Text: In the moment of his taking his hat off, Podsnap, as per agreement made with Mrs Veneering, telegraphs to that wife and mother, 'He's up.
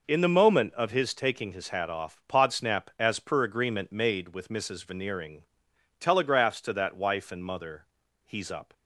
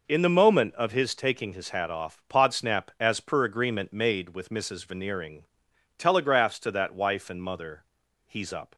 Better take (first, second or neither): neither